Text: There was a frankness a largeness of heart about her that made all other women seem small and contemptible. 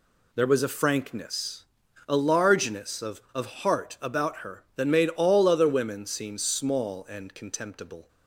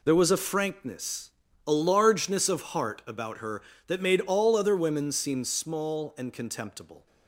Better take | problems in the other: second | pauses between "frankness" and "a"; at 1.6 s; 0.42 s long; slight in the second // says "of" twice; at 3.3 s

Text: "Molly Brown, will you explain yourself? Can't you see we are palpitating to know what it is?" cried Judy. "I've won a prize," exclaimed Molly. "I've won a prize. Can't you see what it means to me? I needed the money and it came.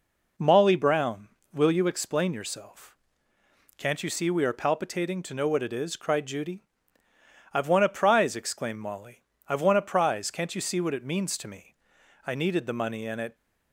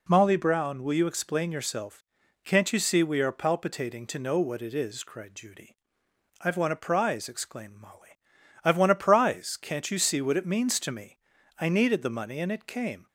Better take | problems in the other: second | stops before "came"; at 13.3 s

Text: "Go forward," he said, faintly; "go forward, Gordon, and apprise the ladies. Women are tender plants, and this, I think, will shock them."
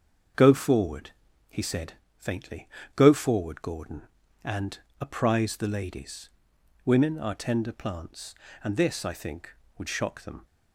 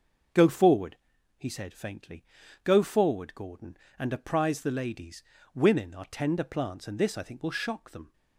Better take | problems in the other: second | starts louder than the rest; until 1.7 s; 6.5 dB // pauses between "and" and "apprise"; slight; at 4.7 s; 0.20 s long // says "would" for "will"; at 9.7 s

